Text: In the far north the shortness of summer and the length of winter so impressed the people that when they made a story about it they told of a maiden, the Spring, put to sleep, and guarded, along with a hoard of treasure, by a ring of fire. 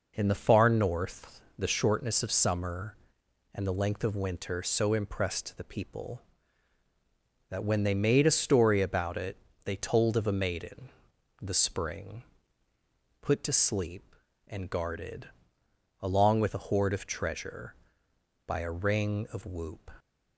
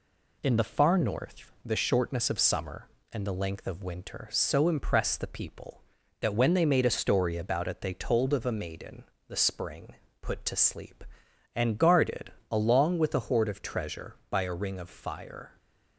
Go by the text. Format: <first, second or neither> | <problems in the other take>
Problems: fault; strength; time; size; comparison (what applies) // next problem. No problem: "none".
second | pauses between "north" and "the"; slight; at 1.4 s; 0.16 s long // pauses between "it" and "they"; slight; at 9.3 s; 0.26 s long // says "whoop" for "fire"; at 19.4 s